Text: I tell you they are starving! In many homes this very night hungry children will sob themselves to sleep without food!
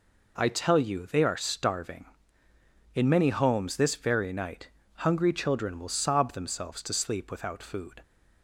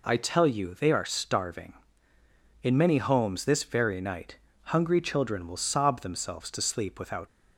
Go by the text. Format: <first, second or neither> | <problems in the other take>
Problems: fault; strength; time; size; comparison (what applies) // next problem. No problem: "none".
first | pauses between "night" and "hungry"; slight; at 4.3 s; 0.28 s long; slight in the first // stops before "food"; at 7.2 s